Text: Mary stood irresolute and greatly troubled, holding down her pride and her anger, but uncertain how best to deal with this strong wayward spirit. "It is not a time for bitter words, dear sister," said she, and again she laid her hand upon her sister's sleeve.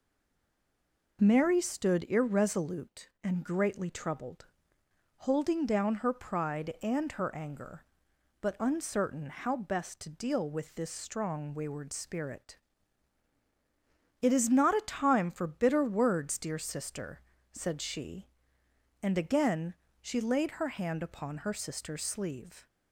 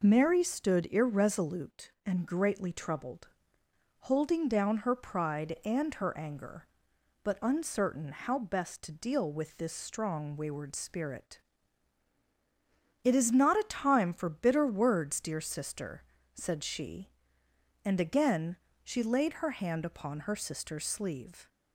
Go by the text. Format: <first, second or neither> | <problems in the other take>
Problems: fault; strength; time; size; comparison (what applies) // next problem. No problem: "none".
second | stays silent before the first word; noticeable; until 1.1 s; 1.1 s long // pauses between "again" and "she"; slight; at 19.7 s; 0.26 s long; slight in the second